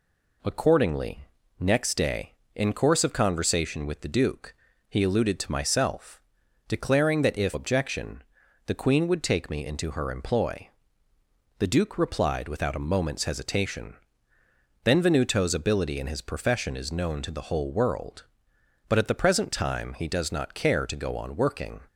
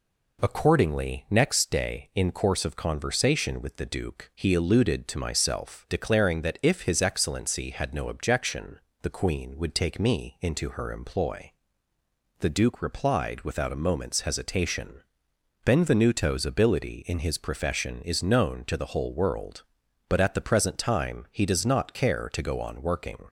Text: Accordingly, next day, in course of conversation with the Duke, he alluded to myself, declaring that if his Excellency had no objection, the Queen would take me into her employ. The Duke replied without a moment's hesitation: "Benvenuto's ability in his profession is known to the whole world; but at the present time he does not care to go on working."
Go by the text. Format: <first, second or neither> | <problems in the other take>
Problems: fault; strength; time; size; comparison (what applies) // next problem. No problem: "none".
second | skips "his Excellency had no"; at 7.5 s